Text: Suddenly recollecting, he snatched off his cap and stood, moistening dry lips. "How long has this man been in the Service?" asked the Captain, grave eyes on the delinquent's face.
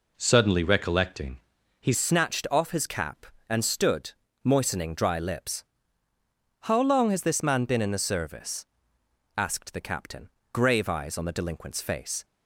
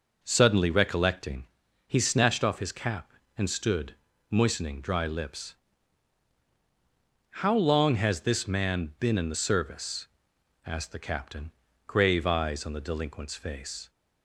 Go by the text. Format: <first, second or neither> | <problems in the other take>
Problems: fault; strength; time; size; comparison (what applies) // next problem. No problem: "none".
second | changes voice at "snatched"; from 1.9 s on; 10.3 s long